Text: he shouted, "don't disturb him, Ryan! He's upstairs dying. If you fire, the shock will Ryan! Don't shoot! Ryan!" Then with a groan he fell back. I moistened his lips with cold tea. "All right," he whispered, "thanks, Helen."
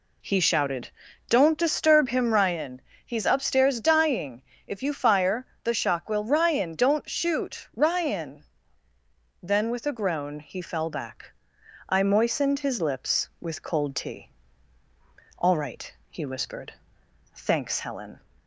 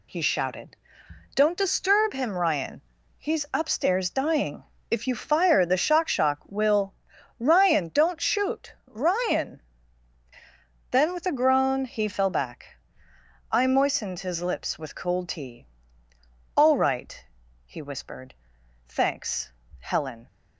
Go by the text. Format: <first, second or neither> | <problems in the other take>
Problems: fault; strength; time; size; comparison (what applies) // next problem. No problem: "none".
first | says "shock" twice; at 6.0 s // pauses between "will" and "Ryan"; noticeable; at 6.9 s; 0.46 s long